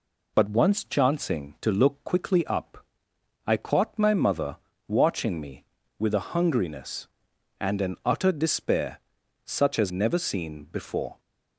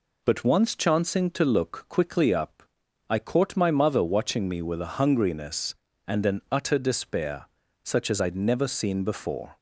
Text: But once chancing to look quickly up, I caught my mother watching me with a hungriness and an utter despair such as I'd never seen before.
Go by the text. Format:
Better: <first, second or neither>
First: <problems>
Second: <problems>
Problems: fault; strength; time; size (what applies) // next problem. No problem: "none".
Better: second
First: pauses between "mother" and "watching"; slight; at 4.5 s; 0.32 s long // pauses between "despair" and "such"; noticeable; at 8.9 s; 0.46 s long // skips "I'd"; at 9.9 s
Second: pauses between "despair" and "such"; at 7.4 s; 0.38 s long